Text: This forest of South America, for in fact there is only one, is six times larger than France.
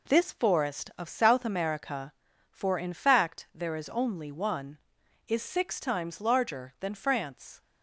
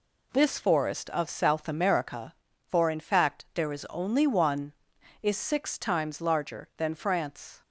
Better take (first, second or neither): neither